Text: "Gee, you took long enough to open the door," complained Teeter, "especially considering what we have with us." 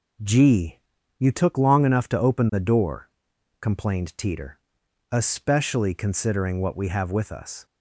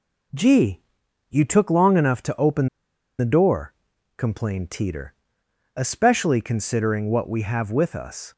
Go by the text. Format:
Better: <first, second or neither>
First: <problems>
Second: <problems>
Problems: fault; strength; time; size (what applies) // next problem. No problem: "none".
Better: first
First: none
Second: pauses between "open" and "the"; noticeable; at 2.6 s; 0.50 s long